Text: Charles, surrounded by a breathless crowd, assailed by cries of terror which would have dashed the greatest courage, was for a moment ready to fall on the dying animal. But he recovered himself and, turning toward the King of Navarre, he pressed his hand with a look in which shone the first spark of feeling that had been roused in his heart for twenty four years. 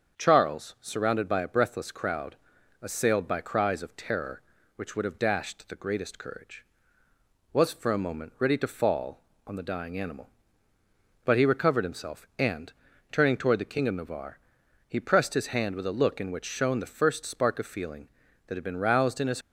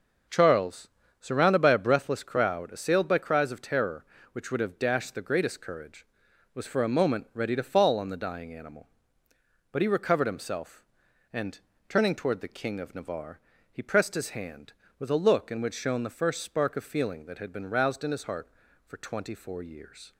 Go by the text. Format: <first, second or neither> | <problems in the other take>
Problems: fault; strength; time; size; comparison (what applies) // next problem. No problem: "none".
second | starts louder than the rest; strong; until 1.2 s; 7 dB // stops before "heart for twenty four years"; at 19.4 s